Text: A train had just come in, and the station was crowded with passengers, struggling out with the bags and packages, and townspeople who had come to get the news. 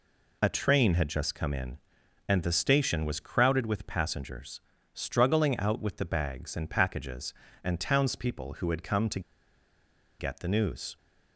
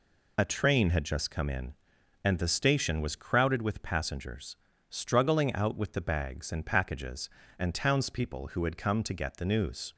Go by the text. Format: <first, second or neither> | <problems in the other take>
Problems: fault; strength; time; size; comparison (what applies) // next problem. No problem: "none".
second | pauses between "to" and "get"; at 9.1 s; 0.99 s long